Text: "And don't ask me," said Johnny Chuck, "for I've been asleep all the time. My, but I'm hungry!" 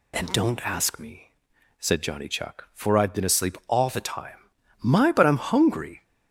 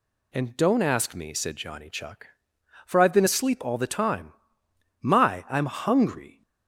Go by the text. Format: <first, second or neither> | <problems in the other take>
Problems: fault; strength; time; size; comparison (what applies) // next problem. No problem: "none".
first | skips "but"; at 5.4 s